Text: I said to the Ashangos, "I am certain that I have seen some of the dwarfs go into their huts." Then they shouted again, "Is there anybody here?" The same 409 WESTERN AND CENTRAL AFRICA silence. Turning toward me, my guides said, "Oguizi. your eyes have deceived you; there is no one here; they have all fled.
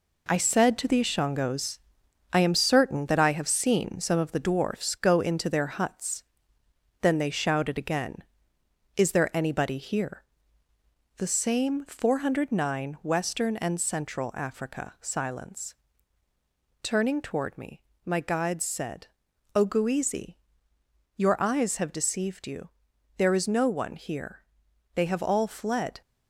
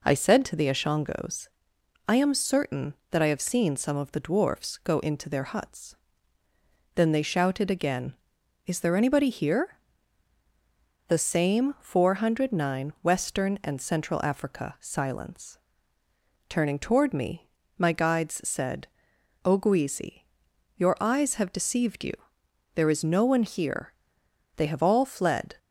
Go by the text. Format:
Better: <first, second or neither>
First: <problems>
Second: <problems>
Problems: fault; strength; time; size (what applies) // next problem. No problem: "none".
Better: second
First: gets quieter; noticeable; throughout; 6 dB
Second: none